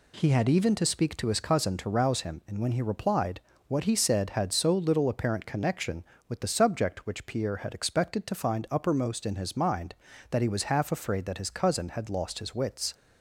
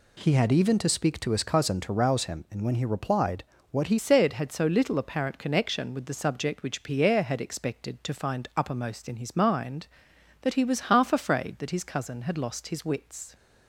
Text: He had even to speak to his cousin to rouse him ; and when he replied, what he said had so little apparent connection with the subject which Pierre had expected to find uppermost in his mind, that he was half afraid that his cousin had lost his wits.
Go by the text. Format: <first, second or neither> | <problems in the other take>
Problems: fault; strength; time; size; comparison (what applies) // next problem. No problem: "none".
first | changes voice at "said"; from 3.9 s on; 9.4 s long